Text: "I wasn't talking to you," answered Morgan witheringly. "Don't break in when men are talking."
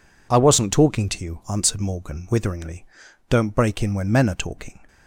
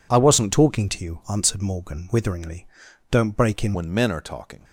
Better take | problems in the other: first | changes voice at "when"; from 3.7 s on; 0.9 s long

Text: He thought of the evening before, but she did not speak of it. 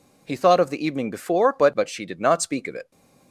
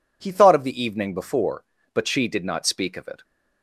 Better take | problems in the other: second | says "but" twice; at 1.7 s

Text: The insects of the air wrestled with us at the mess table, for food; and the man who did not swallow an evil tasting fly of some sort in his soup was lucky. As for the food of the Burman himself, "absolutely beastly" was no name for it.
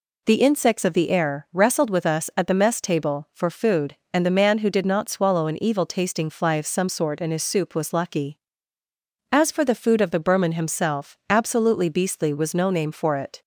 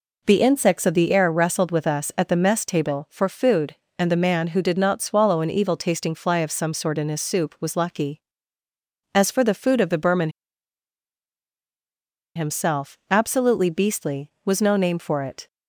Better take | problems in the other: first | pauses between "Burman" and "himself"; strong; at 10.2 s; 2.0 s long

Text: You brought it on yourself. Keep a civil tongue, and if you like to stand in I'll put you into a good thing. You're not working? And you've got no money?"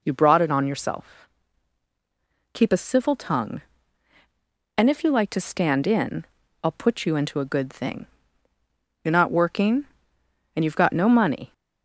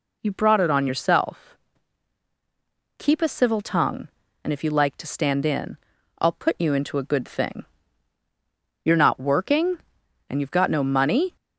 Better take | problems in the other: neither | pauses between "in" and "I'll"; the same in both

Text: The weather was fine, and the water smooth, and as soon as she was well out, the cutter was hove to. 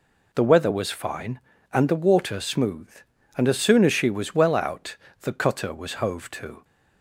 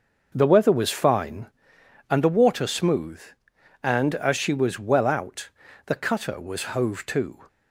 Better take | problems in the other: first | skips "soon as"; at 4.3 s

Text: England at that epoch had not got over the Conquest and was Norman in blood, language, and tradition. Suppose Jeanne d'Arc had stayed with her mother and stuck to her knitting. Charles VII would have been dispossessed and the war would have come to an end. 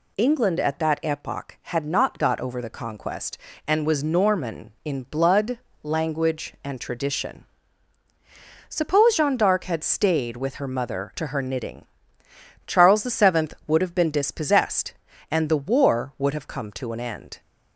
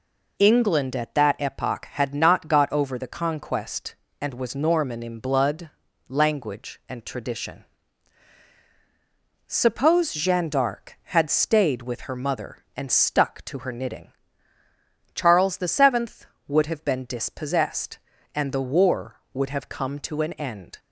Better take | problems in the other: second | skips "and stuck"; at 11.1 s

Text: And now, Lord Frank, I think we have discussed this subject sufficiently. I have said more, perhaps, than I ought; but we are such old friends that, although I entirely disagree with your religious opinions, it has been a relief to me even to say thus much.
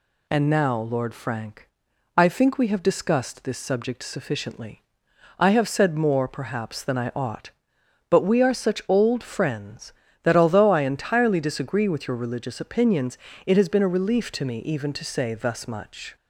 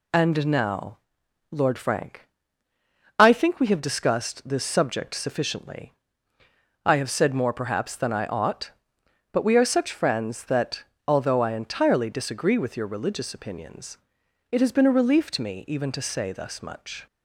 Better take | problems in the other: first | skips "old"; at 9.9 s

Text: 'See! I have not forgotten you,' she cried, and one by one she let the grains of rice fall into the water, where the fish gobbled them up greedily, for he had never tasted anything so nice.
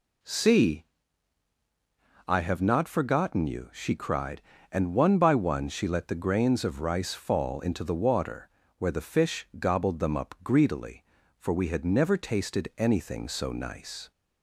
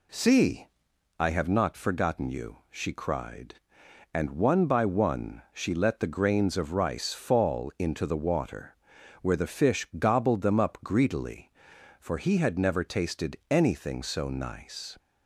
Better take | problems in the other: second | says "we" for "he"; at 11.5 s

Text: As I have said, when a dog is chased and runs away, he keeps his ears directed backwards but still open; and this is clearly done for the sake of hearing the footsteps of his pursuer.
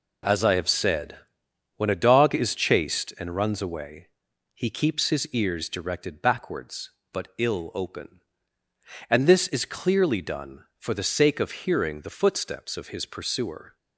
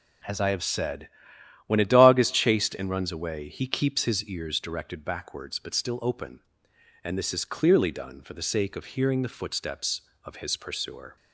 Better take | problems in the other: second | says "ill" for "still"; at 7.3 s

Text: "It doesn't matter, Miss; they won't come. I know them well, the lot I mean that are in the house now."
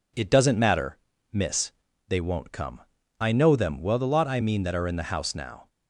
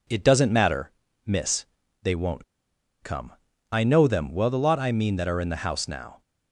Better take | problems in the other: first | pauses between "won't" and "come"; noticeable; at 2.4 s; 0.58 s long

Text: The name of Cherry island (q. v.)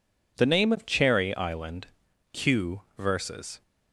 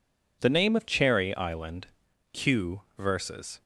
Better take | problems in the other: neither | none

